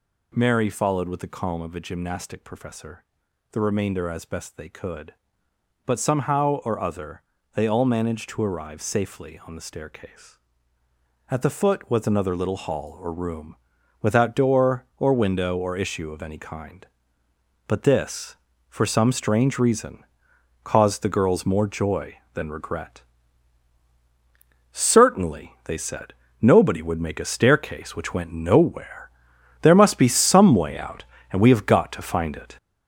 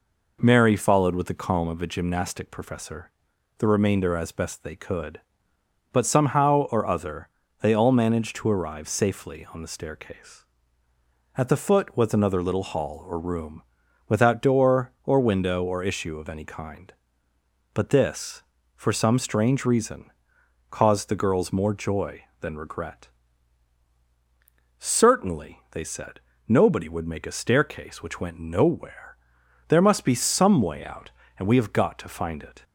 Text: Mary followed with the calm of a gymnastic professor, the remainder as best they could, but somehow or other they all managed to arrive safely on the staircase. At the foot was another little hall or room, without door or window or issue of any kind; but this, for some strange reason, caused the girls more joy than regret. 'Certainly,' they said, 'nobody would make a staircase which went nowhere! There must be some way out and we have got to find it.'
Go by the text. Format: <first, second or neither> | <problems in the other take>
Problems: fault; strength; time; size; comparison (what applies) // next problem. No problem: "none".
second | gets louder; noticeable; throughout; 5.5 dB // pauses between "other" and "they"; slight; at 7.2 s; 0.34 s long; slight in the second